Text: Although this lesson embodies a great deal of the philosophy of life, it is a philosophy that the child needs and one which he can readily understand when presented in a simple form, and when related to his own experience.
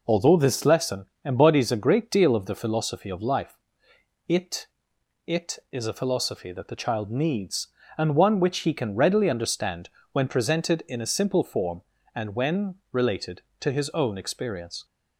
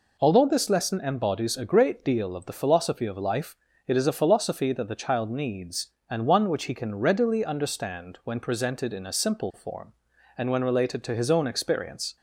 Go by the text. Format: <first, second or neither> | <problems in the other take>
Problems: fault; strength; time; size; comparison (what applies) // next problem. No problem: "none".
second | pauses between "lesson" and "embodies"; slight; at 1.0 s; 0.18 s long // says "it" twice; at 5.2 s // pauses between "understand" and "when"; slight; at 9.8 s; 0.22 s long // pauses between "when" and "related"; slight; at 12.7 s; 0.16 s long